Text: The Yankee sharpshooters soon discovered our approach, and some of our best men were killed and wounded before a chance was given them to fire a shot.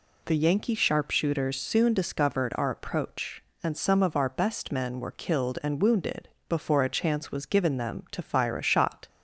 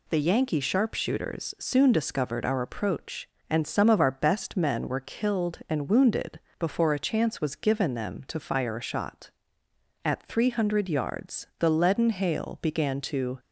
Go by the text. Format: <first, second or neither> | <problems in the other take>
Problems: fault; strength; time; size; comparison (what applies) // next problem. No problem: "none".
first | pauses between "wounded" and "before"; slight; at 6.3 s; 0.20 s long; slight in the first // goes on to say "At three hundred yards the leaden hail began to"; strong; from 10.0 s on; 3.3 s long